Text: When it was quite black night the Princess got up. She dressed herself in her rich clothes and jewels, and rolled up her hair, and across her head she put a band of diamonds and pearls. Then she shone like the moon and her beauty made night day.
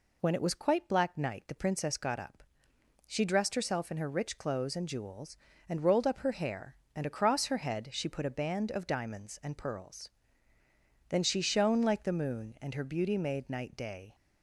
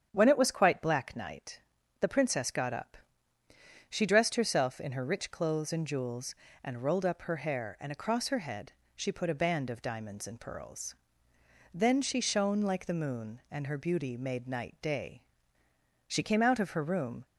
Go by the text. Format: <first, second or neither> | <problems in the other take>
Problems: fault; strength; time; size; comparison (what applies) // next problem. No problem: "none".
first | starts louder than the rest; strong; until 1.1 s; 8 dB // pauses between "night" and "the"; at 1.5 s; 0.42 s long // pauses between "head" and "she"; slight; at 8.7 s; 0.24 s long // goes on to say "She came out of her room"; noticeable; from 16.0 s on; 1.1 s long